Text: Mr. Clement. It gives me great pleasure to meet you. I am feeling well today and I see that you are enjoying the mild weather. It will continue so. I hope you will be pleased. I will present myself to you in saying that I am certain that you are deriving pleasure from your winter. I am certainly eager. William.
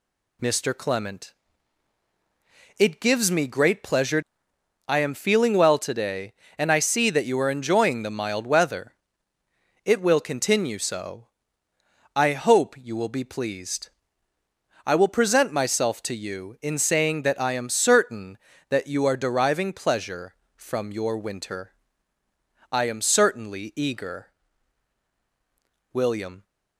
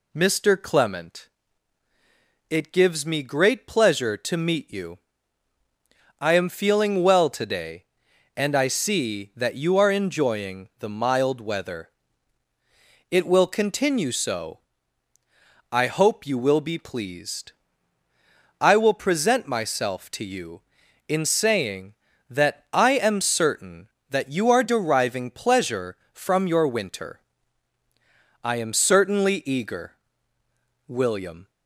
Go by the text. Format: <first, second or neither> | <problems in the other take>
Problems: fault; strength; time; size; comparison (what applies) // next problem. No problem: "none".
second | skips "to meet you"; at 4.5 s